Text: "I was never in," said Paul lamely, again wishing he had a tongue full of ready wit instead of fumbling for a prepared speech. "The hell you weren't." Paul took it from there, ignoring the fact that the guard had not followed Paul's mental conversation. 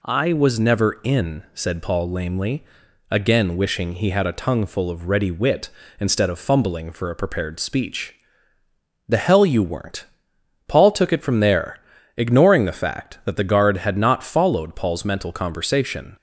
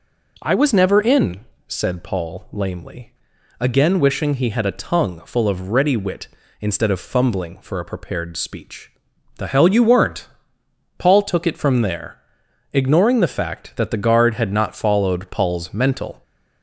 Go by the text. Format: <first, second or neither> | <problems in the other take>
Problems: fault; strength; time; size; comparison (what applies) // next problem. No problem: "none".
first | stops before "conversation"; at 16.2 s